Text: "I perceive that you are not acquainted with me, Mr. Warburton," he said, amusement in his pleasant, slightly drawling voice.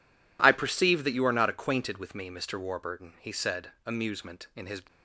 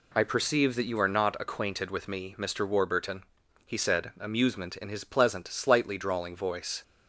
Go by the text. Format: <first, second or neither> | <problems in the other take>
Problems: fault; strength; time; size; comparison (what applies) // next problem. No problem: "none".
second | stops before "pleasant slightly drawling voice"; at 4.8 s